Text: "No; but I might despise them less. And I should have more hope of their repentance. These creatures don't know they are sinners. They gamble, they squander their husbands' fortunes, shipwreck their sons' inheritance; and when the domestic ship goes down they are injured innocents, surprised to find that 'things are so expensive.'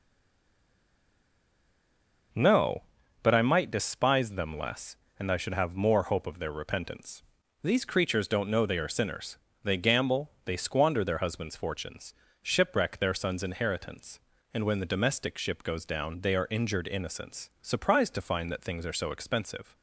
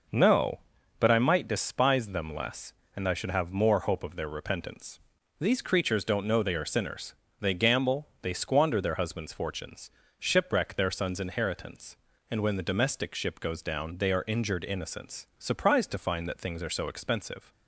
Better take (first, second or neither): second